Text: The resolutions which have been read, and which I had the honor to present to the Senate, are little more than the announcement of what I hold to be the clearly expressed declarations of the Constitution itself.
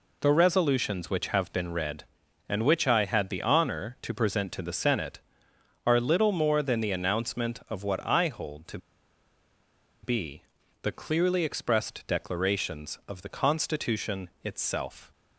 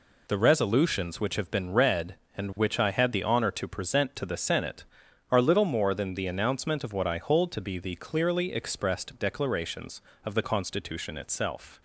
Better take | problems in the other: second | pauses between "to" and "be"; strong; at 8.7 s; 1.2 s long // pauses between "be" and "the"; at 10.4 s; 0.40 s long

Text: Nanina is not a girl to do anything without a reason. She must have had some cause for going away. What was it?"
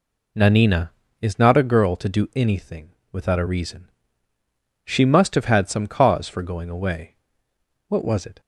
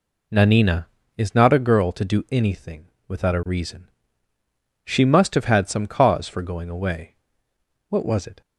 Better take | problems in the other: neither | pauses between "anything" and "without"; slight; the same in both

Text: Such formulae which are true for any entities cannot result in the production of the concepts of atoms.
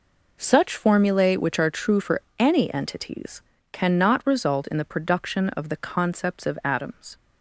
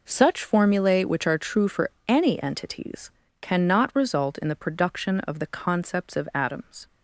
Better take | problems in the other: neither | pauses between "for" and "any"; slight; the same in both // pauses between "entities" and "cannot"; slight; the same in both

